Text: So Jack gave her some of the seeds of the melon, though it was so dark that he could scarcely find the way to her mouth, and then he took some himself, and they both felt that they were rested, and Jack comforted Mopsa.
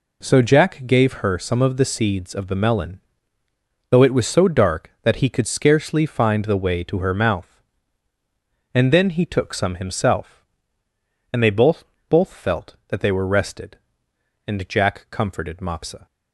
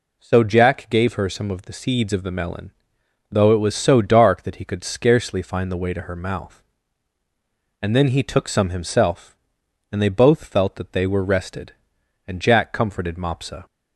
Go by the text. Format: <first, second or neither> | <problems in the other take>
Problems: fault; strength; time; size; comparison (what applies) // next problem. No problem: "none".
second | says "both" twice; at 12.0 s